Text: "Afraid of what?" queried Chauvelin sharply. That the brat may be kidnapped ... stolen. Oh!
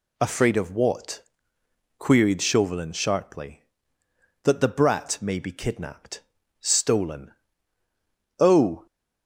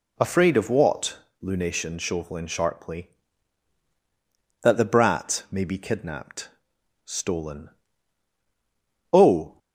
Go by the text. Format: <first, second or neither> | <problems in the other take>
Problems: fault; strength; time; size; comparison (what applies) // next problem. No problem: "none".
first | says "lunation" for "queried"; at 1.4 s